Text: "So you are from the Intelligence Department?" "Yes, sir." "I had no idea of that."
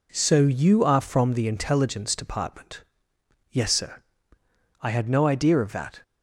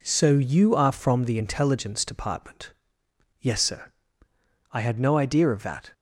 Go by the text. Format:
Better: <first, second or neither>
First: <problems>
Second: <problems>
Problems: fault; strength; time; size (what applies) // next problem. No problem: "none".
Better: neither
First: none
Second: none